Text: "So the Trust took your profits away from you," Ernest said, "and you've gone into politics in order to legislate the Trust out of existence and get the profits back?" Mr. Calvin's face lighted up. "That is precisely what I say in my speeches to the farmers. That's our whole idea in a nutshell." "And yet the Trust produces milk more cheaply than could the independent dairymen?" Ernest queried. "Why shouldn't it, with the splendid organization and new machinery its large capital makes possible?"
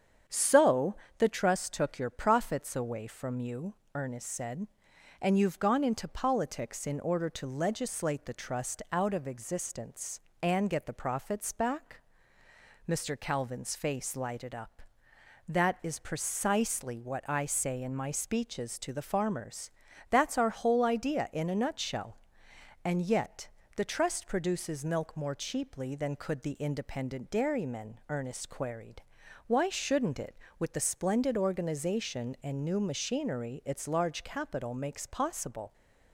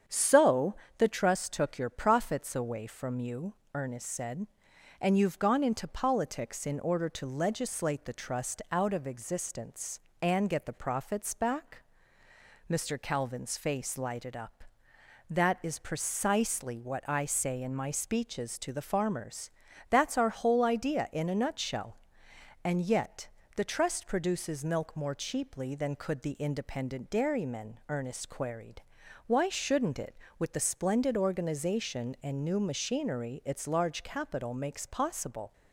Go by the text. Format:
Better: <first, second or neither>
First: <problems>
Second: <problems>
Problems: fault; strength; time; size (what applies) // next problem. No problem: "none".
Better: neither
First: starts louder than the rest; strong; until 1.5 s; 8 dB // pauses between "So" and "the"; slight; at 0.9 s; 0.24 s long // pauses between "yet" and "the"; slight; at 23.4 s; 0.26 s long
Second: starts louder than the rest; strong; until 1.3 s; 8 dB // pauses between "So" and "the"; slight; at 0.7 s; 0.24 s long // pauses between "yet" and "the"; slight; at 23.2 s; 0.26 s long